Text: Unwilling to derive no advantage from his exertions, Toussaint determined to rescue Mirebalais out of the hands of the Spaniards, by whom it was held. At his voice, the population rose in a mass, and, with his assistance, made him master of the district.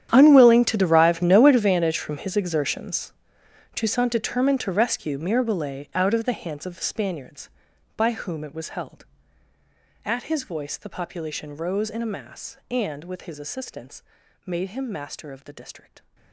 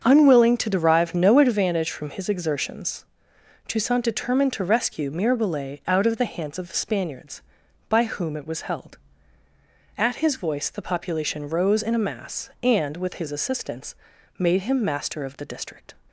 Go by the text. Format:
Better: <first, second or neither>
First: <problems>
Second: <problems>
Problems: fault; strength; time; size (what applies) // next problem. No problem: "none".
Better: second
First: gets quieter; strong; throughout; 18.5 dB // starts louder than the rest; strong; until 1.1 s; 10 dB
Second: starts louder than the rest; until 1.0 s; 7 dB